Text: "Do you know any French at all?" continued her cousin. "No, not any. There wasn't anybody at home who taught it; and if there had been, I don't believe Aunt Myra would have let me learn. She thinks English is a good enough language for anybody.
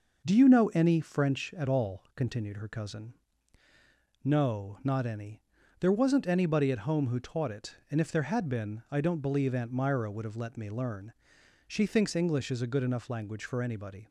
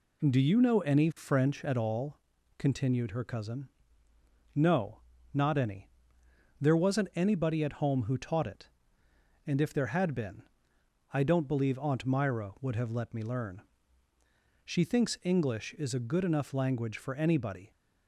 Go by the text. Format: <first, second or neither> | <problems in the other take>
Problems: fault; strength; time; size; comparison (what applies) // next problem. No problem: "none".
neither | none